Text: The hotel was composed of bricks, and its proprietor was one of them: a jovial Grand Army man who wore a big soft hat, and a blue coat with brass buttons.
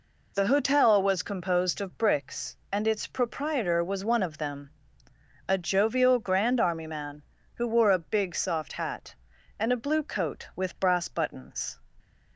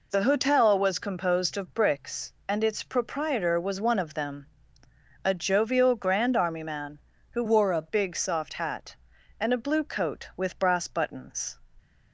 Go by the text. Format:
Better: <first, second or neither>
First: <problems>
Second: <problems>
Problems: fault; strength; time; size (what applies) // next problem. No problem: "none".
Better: first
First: none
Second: changes voice from "wore" to "a"; from 7.4 to 7.8 s; 0.4 s long